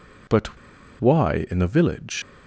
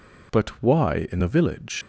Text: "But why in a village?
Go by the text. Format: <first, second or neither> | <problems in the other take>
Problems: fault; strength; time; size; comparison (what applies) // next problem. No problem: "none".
second | pauses between "But" and "why"; at 0.5 s; 0.42 s long